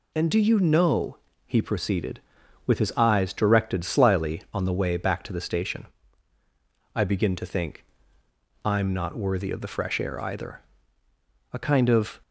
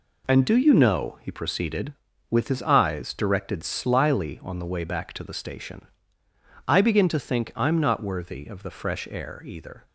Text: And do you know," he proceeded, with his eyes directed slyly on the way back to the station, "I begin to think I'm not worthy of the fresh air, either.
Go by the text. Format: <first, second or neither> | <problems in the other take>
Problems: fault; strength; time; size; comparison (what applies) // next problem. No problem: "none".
second | pauses between "think" and "I'm"; noticeable; at 7.8 s; 0.80 s long // goes on to say "A kind of"; noticeable; from 11.5 s on; 0.68 s long